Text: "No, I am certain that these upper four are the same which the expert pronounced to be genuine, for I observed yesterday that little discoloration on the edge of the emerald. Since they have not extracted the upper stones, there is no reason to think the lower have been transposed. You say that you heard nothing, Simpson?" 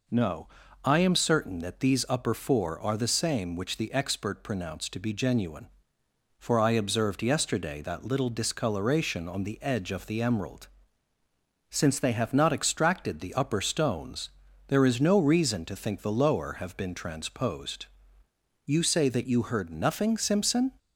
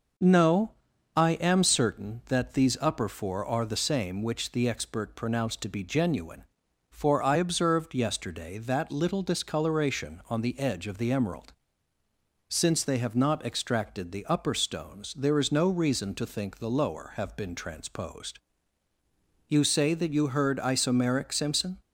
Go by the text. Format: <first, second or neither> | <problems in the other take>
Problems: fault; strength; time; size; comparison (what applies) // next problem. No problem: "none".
first | says "isomeric" for "nothing"; at 20.5 s